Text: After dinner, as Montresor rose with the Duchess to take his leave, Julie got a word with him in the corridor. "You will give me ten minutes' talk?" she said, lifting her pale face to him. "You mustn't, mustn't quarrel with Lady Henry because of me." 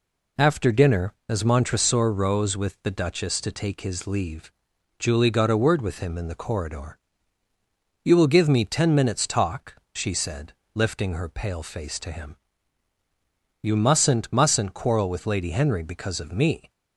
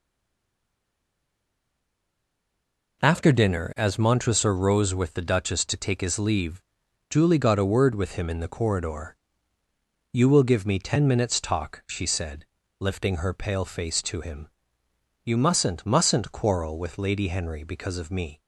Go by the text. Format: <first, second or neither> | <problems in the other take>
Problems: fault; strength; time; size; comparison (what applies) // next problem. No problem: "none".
first | stays silent before the first word; strong; until 3.0 s; 3.0 s long